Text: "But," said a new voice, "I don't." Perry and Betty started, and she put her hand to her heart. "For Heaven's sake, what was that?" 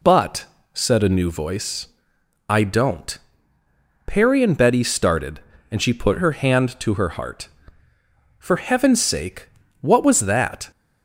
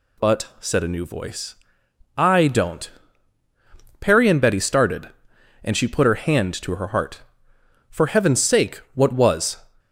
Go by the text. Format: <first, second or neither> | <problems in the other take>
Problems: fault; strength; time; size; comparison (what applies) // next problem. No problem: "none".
first | stops before "that"; at 9.7 s